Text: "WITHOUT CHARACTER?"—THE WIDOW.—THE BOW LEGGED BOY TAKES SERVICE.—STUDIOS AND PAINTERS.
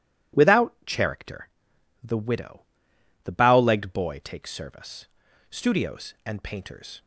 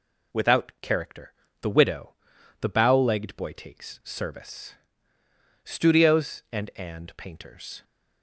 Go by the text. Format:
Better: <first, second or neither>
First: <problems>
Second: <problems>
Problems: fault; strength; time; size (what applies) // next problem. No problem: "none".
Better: first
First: none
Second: says "AND" twice; at 6.7 s